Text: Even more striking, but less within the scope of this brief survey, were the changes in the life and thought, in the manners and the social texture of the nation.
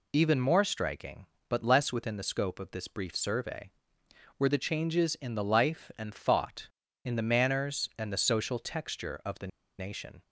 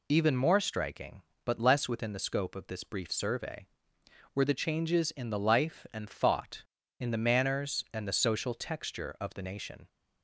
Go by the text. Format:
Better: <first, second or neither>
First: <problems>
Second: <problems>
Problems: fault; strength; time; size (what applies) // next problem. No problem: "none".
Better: second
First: pauses between "the" and "nation"; slight; at 9.4 s; 0.31 s long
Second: none